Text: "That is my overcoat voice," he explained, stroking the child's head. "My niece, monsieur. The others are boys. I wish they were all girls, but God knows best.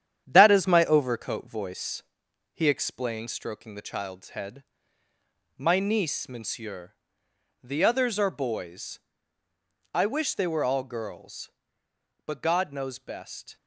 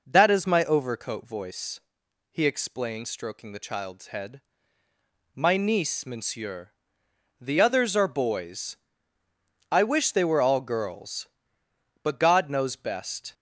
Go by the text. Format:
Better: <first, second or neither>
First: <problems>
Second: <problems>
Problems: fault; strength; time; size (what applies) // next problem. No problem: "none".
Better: second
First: gets quieter; noticeable; throughout; 4.5 dB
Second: none